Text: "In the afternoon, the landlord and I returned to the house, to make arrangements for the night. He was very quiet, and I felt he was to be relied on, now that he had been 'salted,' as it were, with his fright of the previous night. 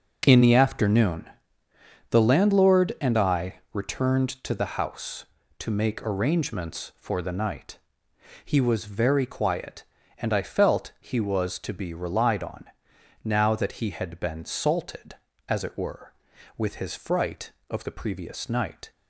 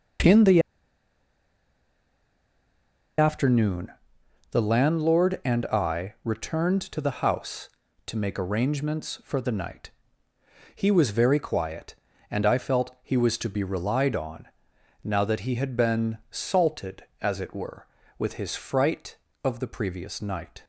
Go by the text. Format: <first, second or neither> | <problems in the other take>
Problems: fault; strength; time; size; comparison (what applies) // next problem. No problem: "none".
first | pauses between "the" and "afternoon"; strong; at 0.6 s; 2.5 s long